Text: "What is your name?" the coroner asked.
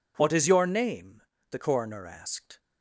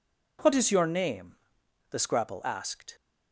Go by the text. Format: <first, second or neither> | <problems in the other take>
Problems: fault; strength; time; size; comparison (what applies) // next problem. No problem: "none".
first | says "scrapple" for "coroner"; at 1.9 s